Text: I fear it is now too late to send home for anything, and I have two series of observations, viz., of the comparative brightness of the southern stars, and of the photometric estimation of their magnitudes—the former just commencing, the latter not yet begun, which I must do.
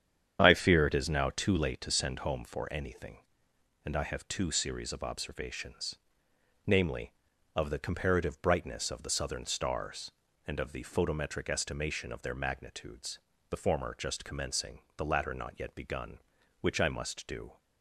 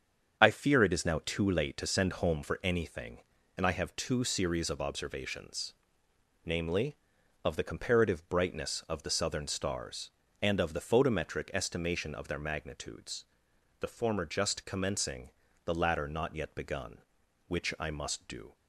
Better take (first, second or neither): neither